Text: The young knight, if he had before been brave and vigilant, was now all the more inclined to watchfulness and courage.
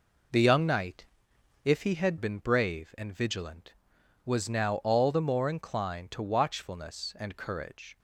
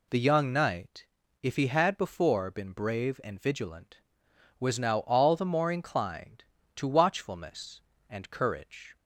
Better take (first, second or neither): second